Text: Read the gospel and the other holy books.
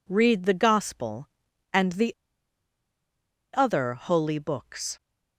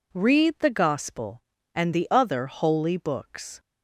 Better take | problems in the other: second | pauses between "the" and "other"; strong; at 2.1 s; 1.3 s long

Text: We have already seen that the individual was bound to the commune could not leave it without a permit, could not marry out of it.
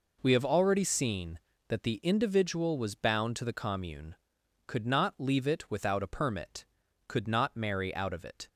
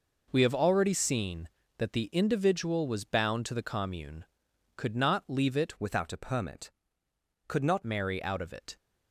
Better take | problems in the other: first | changes voice from "without" to "not"; from 5.7 to 7.8 s; 2.1 s long

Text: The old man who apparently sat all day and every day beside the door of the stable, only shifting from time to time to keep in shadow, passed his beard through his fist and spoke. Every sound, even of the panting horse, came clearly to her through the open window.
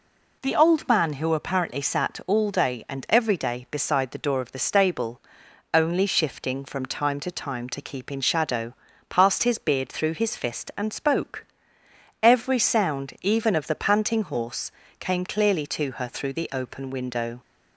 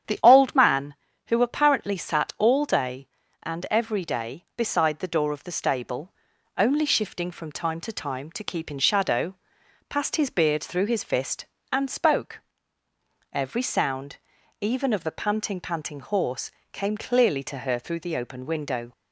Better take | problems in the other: first | starts louder than the rest; strong; until 1.4 s; 9 dB // says "panting" twice; at 15.5 s

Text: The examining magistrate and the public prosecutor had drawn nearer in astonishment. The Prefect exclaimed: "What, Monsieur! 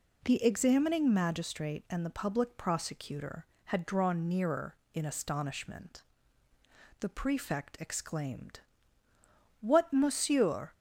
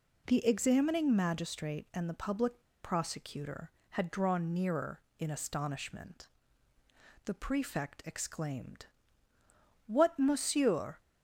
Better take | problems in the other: first | pauses between "public" and "prosecutor"; slight; at 2.6 s; 0.21 s long

